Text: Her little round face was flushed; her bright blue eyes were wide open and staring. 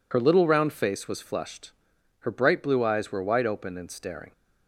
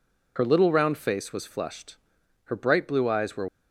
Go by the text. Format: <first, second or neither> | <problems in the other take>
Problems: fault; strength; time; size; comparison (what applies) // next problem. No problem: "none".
first | stops before "wide open and staring"; at 3.4 s